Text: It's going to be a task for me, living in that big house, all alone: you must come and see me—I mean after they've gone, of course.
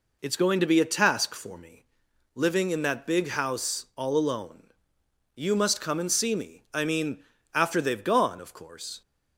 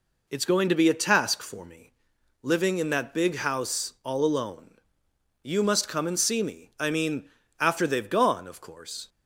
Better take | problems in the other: neither | pauses between "mean" and "after"; slight; the same in both

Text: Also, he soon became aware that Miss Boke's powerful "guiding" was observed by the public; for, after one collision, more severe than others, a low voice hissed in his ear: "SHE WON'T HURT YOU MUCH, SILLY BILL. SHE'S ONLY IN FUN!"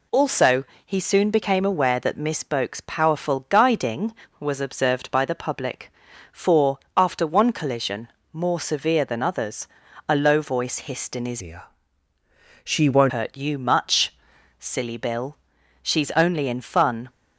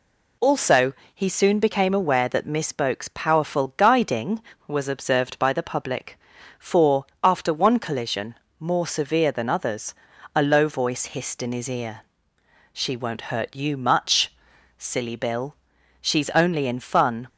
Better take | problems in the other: second | changes voice from "ear" to "WON'T"; from 11.4 to 13.1 s; 1.7 s long

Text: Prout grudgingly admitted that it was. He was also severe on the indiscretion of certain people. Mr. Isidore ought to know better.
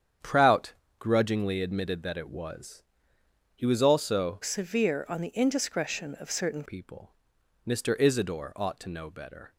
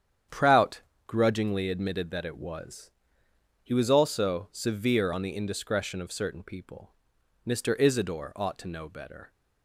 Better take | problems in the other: second | starts louder than the rest; strong; until 1.4 s; 8.5 dB; strong in the second // pauses between "Prout" and "grudgingly"; slight; at 0.7 s; 0.24 s long; slight in the second // changes voice from "severe" to "certain"; from 4.4 to 6.6 s; 2.2 s long

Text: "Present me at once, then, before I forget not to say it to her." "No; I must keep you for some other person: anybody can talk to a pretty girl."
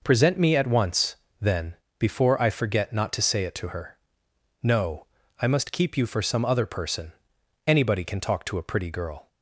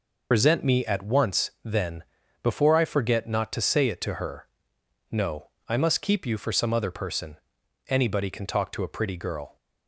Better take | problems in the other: first | loses the start of "Present"; at 0.3 s; 70 ms

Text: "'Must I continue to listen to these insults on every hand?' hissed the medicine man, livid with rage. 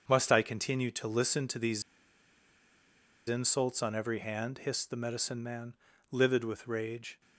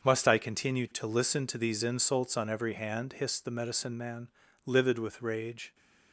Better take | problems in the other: second | starts louder than the rest; until 1.0 s; 6.5 dB; also in the second // pauses between "these" and "insults"; strong; at 1.8 s; 1.4 s long

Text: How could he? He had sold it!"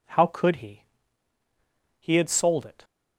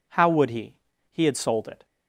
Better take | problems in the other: first | says "would" for "could"; at 0.2 s

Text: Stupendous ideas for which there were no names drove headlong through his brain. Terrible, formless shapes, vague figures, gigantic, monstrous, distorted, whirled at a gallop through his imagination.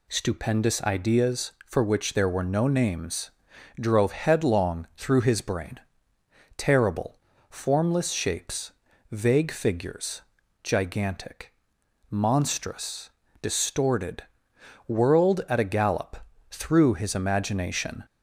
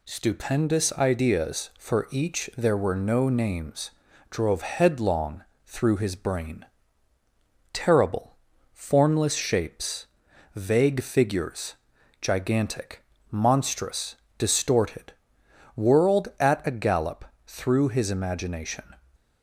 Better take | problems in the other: first | says "each" for "which"; at 2.1 s // pauses between "names" and "drove"; at 3.9 s; 0.40 s long; noticeable in the first // pauses between "headlong" and "through"; slight; at 5.4 s; 0.20 s long // pauses between "gallop" and "through"; slight; at 17.2 s; 0.22 s long; slight in the first

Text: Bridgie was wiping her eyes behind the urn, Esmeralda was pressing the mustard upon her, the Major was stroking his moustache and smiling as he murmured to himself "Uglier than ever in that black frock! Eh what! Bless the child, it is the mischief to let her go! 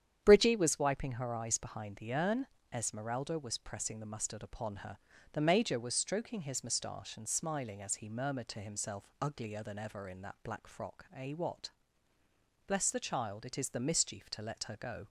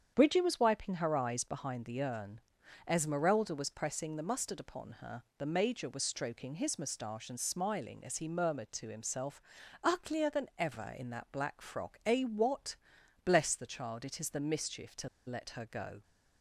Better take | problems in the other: first | starts louder than the rest; strong; until 1.1 s; 8 dB; strong in the first // pauses between "himself" and "Uglier"; at 9.3 s; 0.44 s long // pauses between "to" and "let"; slight; at 15.0 s; 0.18 s long

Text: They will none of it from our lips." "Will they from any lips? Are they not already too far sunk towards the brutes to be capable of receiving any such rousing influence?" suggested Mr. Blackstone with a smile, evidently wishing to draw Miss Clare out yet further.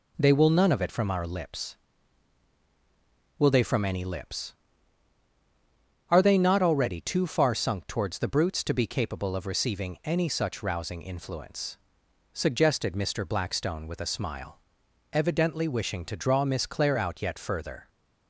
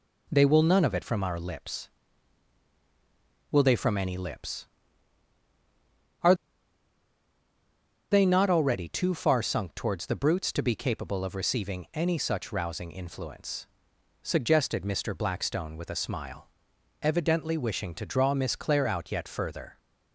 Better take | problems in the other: first | pauses between "Are" and "they"; strong; at 6.3 s; 1.7 s long

